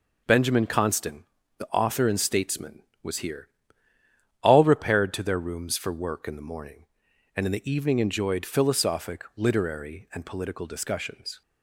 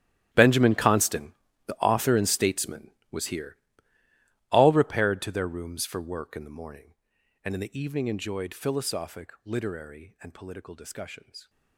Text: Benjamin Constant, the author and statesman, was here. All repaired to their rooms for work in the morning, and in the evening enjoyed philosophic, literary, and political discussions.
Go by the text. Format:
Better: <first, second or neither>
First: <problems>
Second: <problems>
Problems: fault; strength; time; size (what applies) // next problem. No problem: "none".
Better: first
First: none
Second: gets quieter; strong; throughout; 17.5 dB